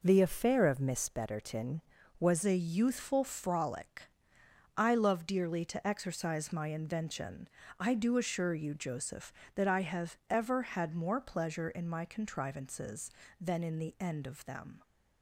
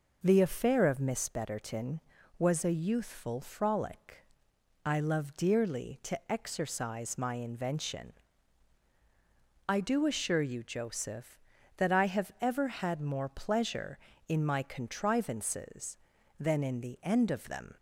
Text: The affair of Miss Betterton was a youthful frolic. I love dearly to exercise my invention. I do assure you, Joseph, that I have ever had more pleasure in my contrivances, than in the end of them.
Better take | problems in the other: second | changes voice at "a"; from 2.4 s on; 12.4 s long

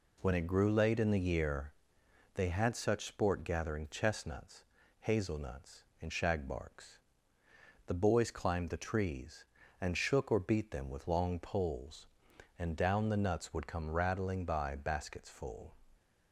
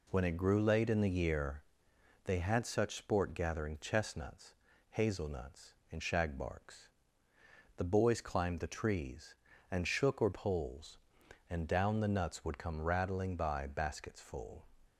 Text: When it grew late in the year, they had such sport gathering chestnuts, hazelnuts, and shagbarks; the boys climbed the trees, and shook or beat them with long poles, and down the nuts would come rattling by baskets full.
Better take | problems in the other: first | skips "beat them with long"; at 10.3 s

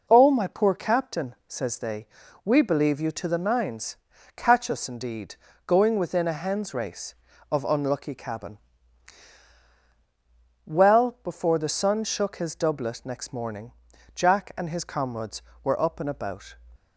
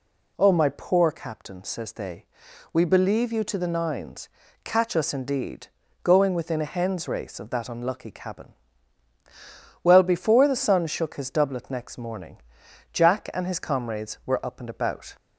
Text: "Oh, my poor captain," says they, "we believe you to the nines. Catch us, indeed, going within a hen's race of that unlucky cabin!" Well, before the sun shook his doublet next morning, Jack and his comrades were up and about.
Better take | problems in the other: second | skips "that"; at 7.6 s

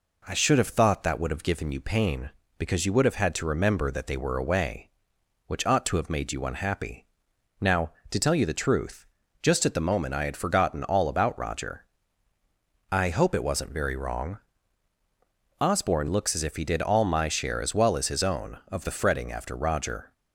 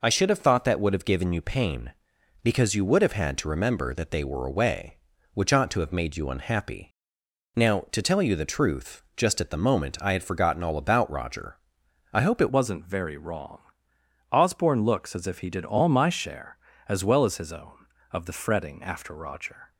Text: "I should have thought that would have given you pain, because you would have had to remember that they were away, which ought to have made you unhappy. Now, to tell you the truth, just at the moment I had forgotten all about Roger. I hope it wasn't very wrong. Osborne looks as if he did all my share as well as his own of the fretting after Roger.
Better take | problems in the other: first | changes voice at "wasn't"; from 12.5 s on; 7.2 s long

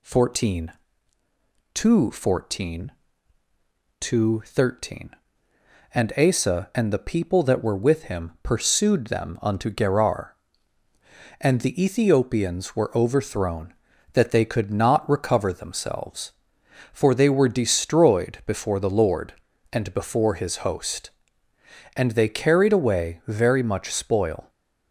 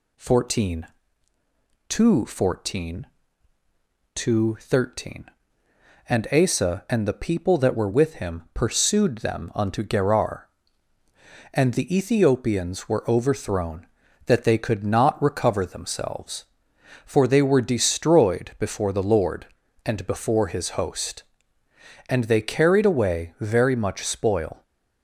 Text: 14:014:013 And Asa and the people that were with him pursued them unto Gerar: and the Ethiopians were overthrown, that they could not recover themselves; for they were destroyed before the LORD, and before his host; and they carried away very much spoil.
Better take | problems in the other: neither | none

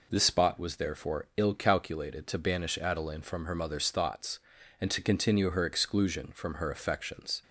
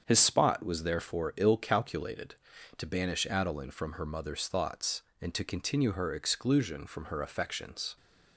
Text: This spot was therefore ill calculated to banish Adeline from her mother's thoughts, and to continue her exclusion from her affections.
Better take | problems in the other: first | starts louder than the rest; strong; until 1.0 s; 7.5 dB // says "His" for "This"; at 0.0 s

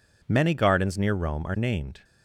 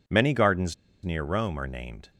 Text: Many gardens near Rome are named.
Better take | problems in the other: first | pauses between "gardens" and "near"; slight; at 0.7 s; 0.29 s long

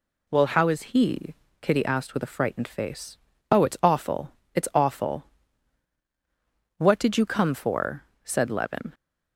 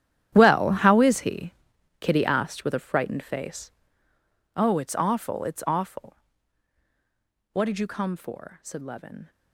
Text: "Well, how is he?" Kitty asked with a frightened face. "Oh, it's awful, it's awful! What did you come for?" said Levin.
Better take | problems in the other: first | gets quieter; strong; throughout; 16.5 dB

